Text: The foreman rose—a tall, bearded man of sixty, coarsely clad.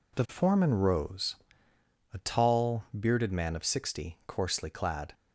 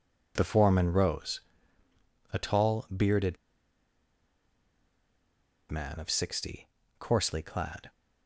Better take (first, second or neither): first